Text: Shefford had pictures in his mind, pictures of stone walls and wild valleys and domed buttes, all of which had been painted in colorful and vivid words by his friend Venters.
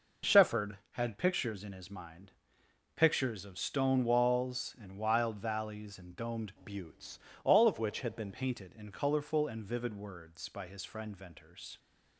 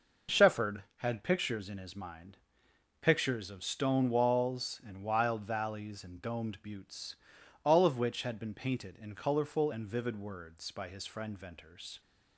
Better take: second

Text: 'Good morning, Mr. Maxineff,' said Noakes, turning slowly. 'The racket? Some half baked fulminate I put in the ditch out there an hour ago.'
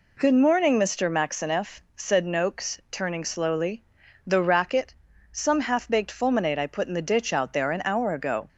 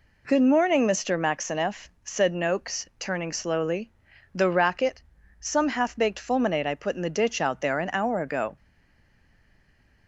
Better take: first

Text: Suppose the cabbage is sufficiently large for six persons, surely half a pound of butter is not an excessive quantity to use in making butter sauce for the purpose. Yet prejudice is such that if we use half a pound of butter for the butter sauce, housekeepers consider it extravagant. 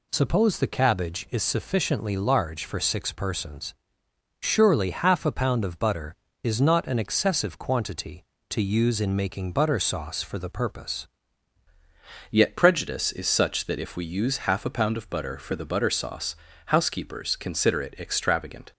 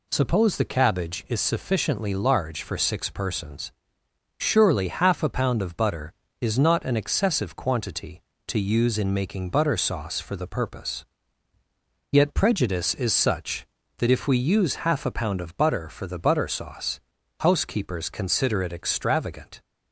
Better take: second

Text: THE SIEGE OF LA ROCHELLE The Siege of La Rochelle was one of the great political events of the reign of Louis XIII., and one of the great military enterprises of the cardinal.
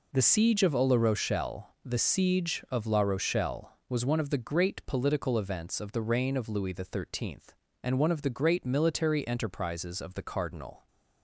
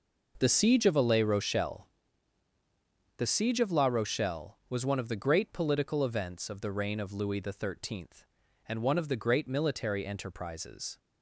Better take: first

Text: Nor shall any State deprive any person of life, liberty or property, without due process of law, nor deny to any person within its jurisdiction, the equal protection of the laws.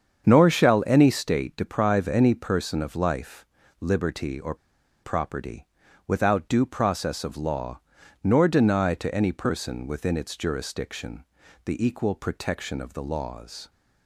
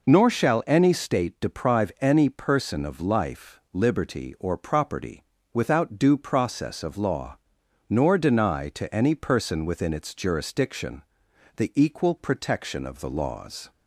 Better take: second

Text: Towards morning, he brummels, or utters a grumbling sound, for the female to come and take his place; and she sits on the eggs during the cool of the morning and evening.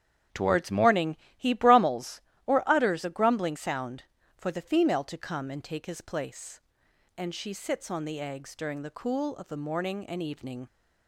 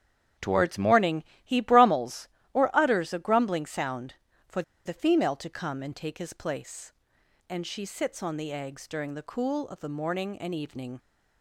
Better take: first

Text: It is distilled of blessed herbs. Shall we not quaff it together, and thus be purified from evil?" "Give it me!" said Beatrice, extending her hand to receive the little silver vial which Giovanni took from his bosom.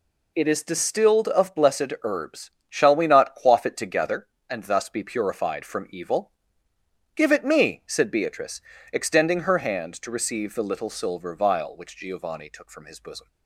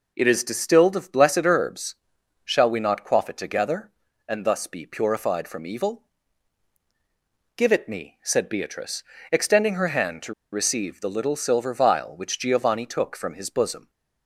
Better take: first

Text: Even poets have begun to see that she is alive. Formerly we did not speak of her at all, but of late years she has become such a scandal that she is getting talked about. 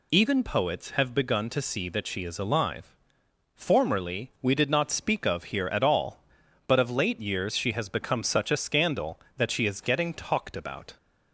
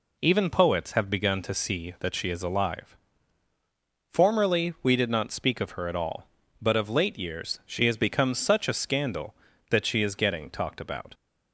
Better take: second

